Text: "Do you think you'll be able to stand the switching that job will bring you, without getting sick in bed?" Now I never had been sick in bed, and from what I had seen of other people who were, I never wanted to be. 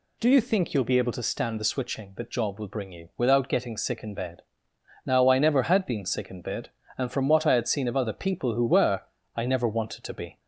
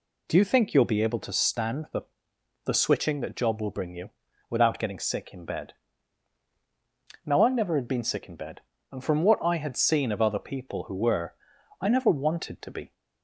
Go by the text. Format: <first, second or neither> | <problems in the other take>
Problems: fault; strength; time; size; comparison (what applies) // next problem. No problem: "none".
first | says "the" twice; at 2.6 s